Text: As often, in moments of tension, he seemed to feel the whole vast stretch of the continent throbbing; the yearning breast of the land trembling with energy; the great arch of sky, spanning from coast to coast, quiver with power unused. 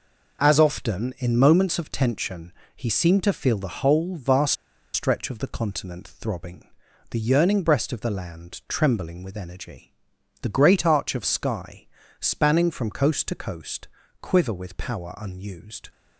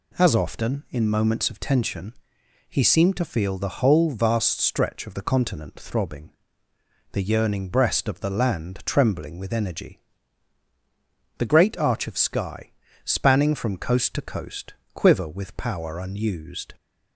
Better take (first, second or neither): second